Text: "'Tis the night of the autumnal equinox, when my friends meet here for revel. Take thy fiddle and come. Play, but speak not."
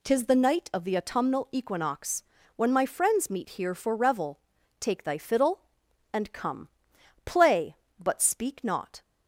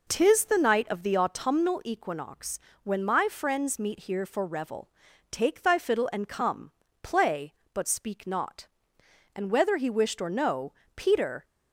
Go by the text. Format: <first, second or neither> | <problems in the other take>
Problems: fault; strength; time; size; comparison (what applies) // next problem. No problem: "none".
first | goes on to say "And whether he wished or no Peter"; strong; from 9.3 s on; 2.0 s long